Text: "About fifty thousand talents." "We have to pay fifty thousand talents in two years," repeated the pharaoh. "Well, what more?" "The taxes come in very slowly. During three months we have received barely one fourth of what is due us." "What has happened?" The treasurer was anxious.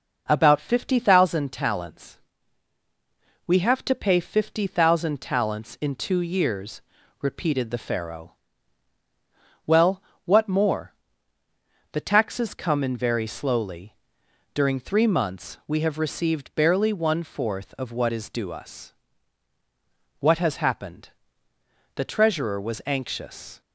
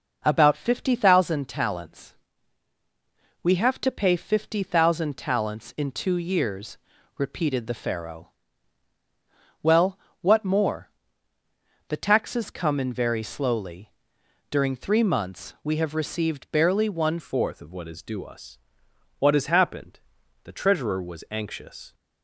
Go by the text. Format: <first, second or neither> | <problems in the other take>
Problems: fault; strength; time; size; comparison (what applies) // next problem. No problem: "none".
first | changes voice at "fourth"; from 17.1 s on; 4.8 s long